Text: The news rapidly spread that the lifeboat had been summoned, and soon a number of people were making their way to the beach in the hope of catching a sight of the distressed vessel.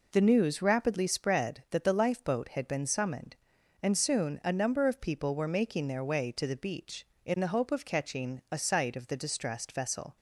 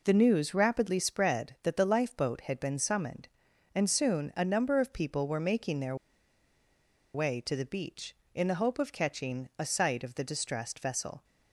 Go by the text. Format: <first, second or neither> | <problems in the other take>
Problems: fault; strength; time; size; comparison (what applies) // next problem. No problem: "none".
first | pauses between "their" and "way"; at 5.9 s; 1.1 s long